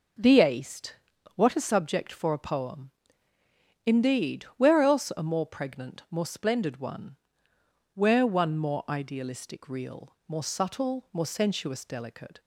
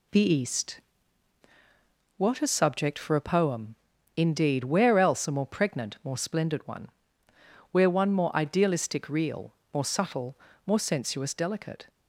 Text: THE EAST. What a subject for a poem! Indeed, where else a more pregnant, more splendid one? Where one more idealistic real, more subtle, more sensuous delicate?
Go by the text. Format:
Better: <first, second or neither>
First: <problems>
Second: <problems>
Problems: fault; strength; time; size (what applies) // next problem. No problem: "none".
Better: neither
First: none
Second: none